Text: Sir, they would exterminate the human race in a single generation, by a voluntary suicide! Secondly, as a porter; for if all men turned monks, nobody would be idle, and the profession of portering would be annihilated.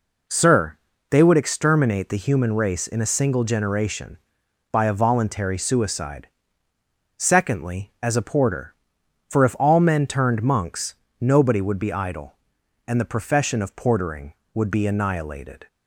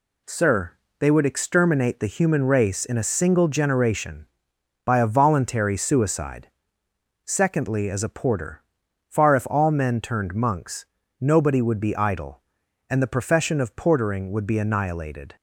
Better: first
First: none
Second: says "far" for "for"; at 9.0 s

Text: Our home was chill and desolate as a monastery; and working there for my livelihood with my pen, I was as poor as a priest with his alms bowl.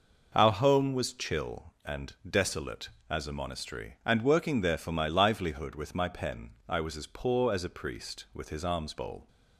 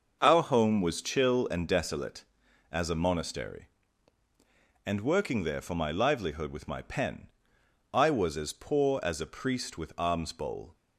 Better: first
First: none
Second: starts louder than the rest; until 1.2 s; 6 dB // skips "his"; at 9.9 s

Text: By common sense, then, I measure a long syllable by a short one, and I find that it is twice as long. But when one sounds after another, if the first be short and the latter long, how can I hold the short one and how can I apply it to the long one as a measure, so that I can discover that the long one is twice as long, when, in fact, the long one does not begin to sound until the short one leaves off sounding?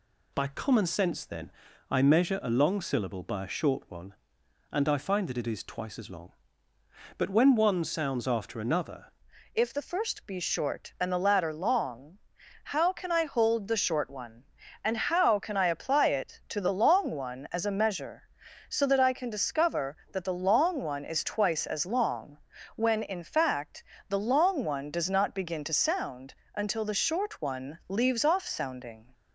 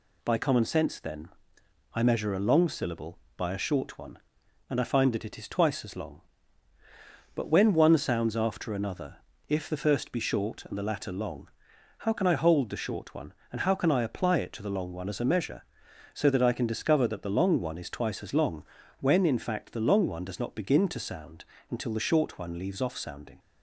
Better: second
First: changes voice at "if"; from 9.5 s on; 19.6 s long // pauses between "sound" and "until"; slight; at 26.3 s; 0.22 s long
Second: pauses between "sound" and "until"; slight; at 21.4 s; 0.26 s long

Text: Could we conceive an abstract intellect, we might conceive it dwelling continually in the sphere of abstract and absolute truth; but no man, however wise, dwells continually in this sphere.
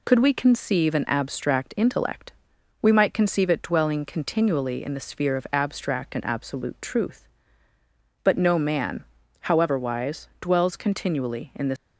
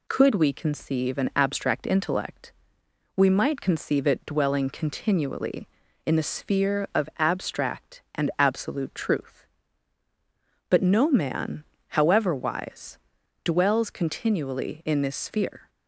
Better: second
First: stops before "sphere"; at 11.7 s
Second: none

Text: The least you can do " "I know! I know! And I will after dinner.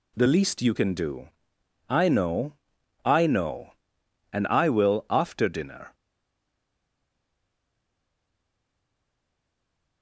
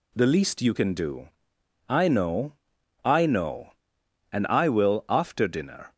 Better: second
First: stays silent after the last word; strong; from 5.9 s on; 4.1 s long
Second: none

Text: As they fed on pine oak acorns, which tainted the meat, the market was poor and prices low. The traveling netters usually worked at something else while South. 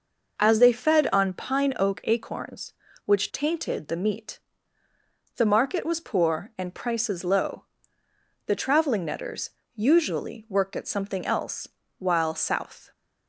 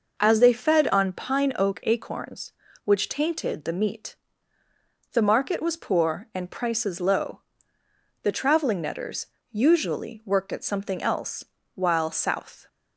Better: neither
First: pauses between "netters" and "usually"; slight; at 9.4 s; 0.26 s long // pauses between "else" and "while"; slight; at 11.6 s; 0.30 s long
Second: pauses between "netters" and "usually"; slight; at 9.2 s; 0.26 s long // pauses between "else" and "while"; slight; at 11.4 s; 0.30 s long

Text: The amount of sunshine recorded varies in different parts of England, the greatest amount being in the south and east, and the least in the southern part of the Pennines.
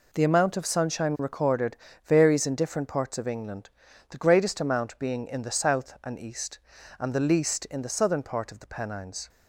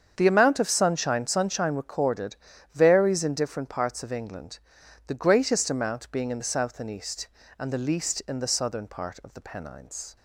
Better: first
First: pauses between "recorded" and "varies"; slight; at 1.7 s; 0.30 s long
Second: starts louder than the rest; strong; until 1.1 s; 7.5 dB // says "sunshine" twice; at 1.2 s // pauses between "recorded" and "varies"; slight; at 2.3 s; 0.36 s long

